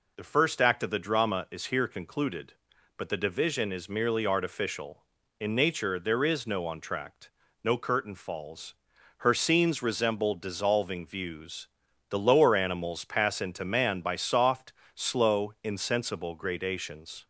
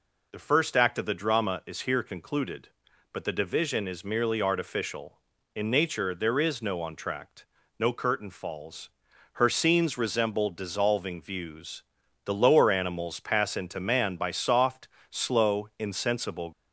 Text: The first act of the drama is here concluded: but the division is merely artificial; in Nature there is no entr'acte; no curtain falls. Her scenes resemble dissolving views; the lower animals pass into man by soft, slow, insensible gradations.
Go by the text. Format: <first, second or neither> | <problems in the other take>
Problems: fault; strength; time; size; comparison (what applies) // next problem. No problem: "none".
first | stops before "gradations"; at 16.5 s